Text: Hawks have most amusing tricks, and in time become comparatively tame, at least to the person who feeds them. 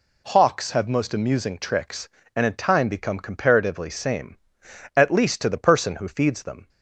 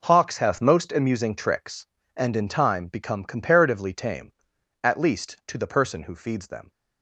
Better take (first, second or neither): second